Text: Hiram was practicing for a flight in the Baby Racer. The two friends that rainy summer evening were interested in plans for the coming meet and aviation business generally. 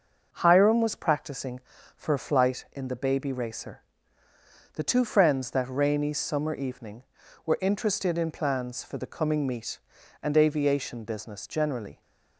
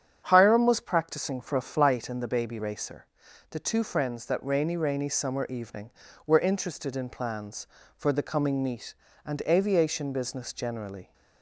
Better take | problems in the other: first | starts louder than the rest; strong; until 1.2 s; 8.5 dB // says "rainy" twice; at 4.7 s

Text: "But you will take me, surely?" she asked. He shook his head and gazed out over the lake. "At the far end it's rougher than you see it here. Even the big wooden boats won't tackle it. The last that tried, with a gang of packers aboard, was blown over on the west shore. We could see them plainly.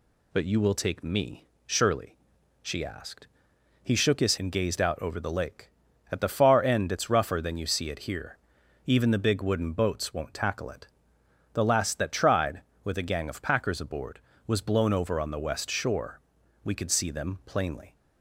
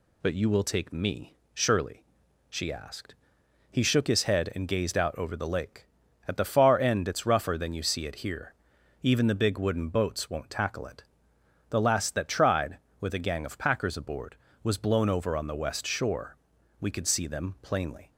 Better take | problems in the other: second | skips "head"; at 4.3 s

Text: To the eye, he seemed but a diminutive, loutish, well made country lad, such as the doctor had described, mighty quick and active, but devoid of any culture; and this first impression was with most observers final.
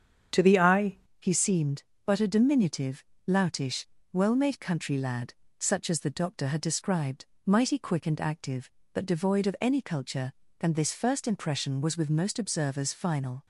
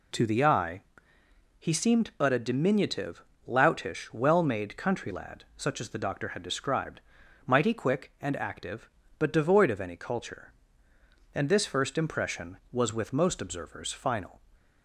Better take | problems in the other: second | starts louder than the rest; strong; until 1.5 s; 8 dB // changes voice at "he"; from 1.2 s on; 12.2 s long

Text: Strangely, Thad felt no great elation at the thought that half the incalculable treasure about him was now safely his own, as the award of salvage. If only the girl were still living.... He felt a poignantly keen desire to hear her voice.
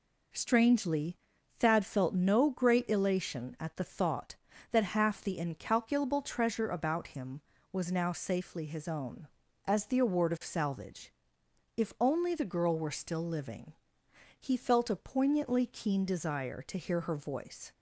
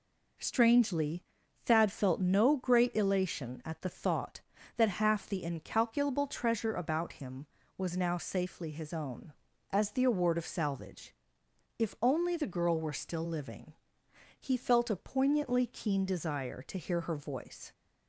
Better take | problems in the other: neither | none

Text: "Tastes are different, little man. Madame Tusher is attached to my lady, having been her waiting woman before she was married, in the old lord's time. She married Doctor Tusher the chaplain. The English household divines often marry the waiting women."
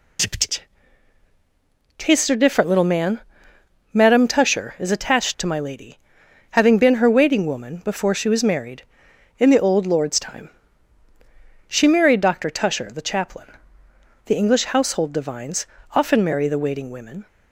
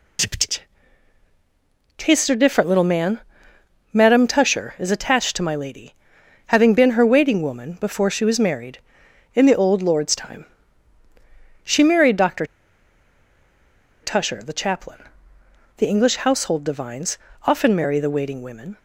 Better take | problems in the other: first | pauses between "Doctor" and "Tusher"; strong; at 12.4 s; 1.5 s long // pauses between "divines" and "often"; slight; at 17.1 s; 0.28 s long; slight in the first

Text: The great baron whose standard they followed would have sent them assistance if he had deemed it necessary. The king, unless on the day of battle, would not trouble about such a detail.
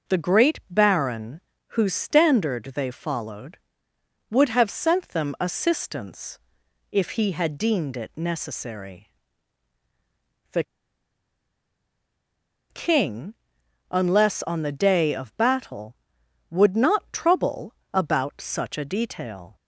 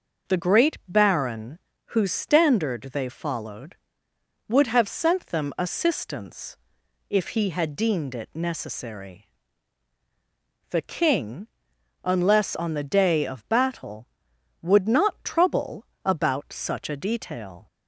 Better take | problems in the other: second | pauses between "baron" and "whose"; slight; at 1.4 s; 0.30 s long; slight in the second // pauses between "assistance" and "if"; noticeable; at 6.3 s; 0.54 s long; noticeable in the second // pauses between "The" and "king"; strong; at 10.6 s; 2.0 s long // pauses between "trouble" and "about"; slight; at 17.7 s; 0.20 s long; slight in the second

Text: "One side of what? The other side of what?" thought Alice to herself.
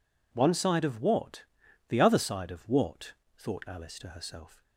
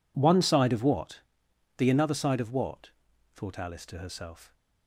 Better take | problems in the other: first | says "another" for "other"; at 1.8 s

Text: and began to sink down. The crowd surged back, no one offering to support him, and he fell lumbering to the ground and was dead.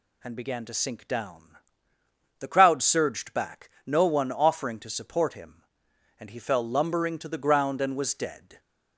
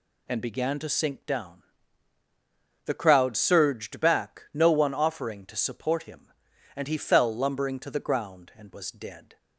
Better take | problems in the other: neither | none

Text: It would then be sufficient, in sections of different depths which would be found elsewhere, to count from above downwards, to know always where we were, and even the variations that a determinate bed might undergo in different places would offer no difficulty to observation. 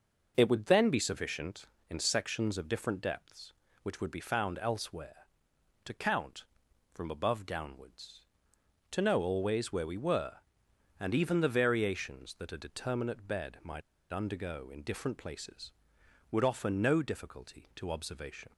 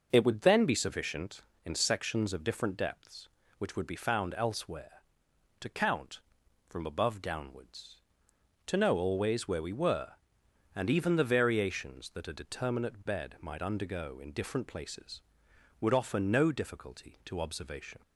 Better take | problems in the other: second | pauses between "might" and "undergo"; slight; at 13.8 s; 0.30 s long

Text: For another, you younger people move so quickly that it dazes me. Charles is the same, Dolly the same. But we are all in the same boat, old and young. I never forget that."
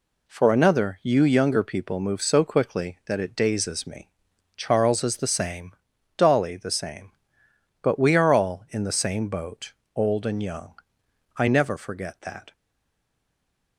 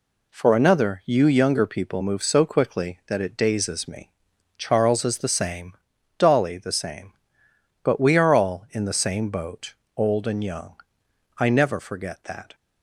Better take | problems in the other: second | stays silent after the last word; noticeable; from 12.5 s on; 1.2 s long

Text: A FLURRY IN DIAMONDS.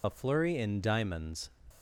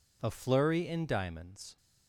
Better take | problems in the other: second | loses the start of "A"; at 0.0 s; 50 ms

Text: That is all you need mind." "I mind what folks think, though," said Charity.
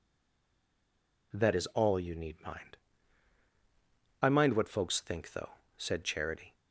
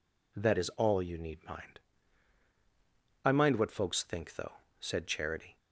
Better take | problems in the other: second | stays silent before the first word; noticeable; until 1.3 s; 1.3 s long

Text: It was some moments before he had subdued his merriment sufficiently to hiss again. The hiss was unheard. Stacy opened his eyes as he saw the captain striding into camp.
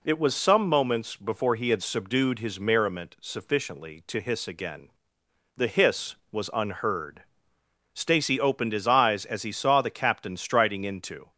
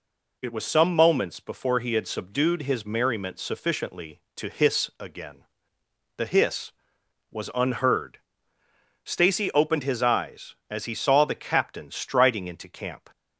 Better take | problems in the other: second | stops before "camp"; at 11.3 s

